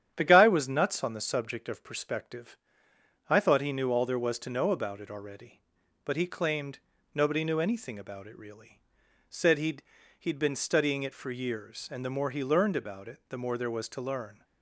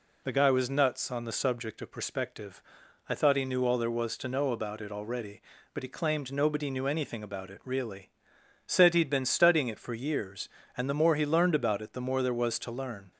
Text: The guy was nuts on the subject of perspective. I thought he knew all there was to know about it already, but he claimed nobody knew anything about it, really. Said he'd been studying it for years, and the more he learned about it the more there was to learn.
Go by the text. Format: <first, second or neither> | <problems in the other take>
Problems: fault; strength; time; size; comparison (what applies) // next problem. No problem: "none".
second | starts louder than the rest; strong; until 1.2 s; 10 dB // pauses between "claimed" and "nobody"; slight; at 6.7 s; 0.34 s long // says "he'd" twice; at 10.1 s